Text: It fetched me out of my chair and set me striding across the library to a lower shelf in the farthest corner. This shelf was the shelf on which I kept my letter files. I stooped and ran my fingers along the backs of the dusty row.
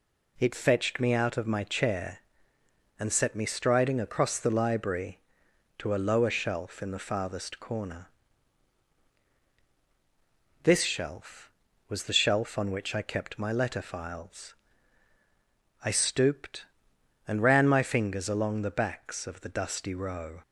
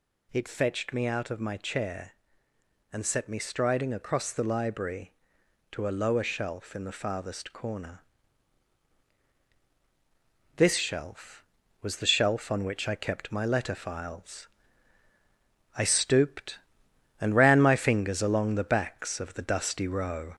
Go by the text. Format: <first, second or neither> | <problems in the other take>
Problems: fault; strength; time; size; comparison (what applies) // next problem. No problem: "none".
first | gets louder; slight; throughout; 2.5 dB